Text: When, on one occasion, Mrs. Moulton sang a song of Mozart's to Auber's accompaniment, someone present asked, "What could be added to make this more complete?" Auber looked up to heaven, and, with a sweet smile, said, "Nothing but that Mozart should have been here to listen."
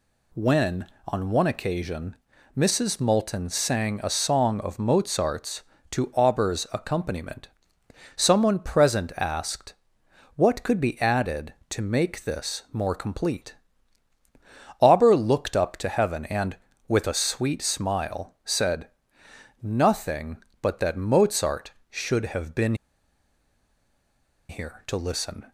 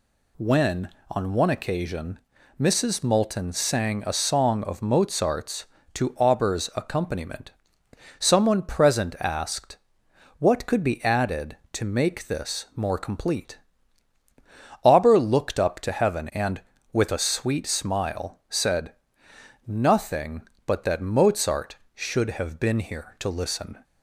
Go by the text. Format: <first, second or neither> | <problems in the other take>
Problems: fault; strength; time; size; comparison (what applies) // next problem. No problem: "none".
second | pauses between "been" and "here"; strong; at 22.7 s; 1.7 s long